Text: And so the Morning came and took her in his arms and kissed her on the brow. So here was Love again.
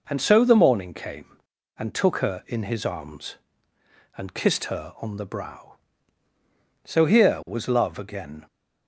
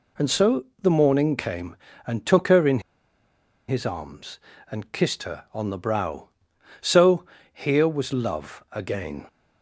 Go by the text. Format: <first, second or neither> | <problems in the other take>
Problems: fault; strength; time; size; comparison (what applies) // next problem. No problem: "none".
first | pauses between "so" and "the"; slight; at 0.6 s; 0.16 s long // pauses between "in" and "his"; noticeable; at 2.8 s; 0.87 s long // pauses between "So" and "here"; slight; at 7.2 s; 0.28 s long